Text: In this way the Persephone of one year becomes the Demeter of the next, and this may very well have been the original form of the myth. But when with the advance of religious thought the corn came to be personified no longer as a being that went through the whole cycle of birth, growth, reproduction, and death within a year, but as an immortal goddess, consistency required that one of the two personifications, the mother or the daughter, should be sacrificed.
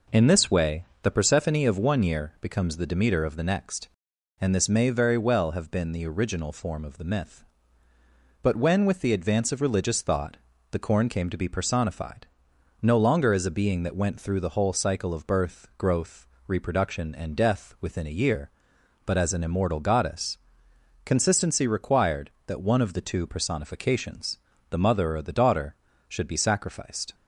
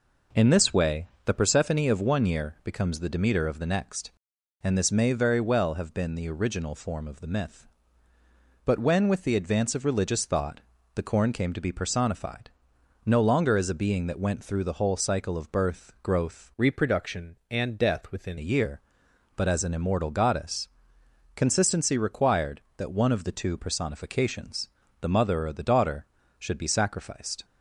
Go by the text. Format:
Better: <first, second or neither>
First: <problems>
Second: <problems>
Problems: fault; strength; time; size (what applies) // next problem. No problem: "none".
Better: first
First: pauses between "way" and "the"; slight; at 0.8 s; 0.18 s long // pauses between "thought" and "the"; slight; at 10.3 s; 0.34 s long // pauses between "personified" and "no"; noticeable; at 12.2 s; 0.54 s long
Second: pauses between "way" and "the"; slight; at 1.0 s; 0.18 s long // pauses between "thought" and "the"; slight; at 10.6 s; 0.34 s long // pauses between "personified" and "no"; noticeable; at 12.4 s; 0.54 s long // changes voice from "reproduction" to "within"; from 16.5 to 18.3 s; 1.8 s long